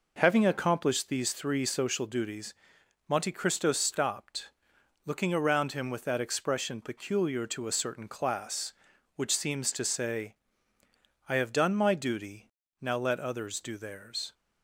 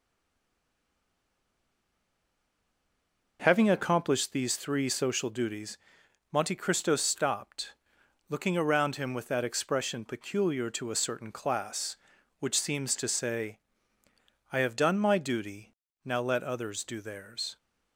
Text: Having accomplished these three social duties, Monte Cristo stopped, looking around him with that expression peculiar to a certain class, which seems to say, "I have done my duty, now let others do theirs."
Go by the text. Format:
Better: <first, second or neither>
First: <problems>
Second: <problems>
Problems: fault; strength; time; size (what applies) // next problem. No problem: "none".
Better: first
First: none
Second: stays silent before the first word; strong; until 3.3 s; 3.3 s long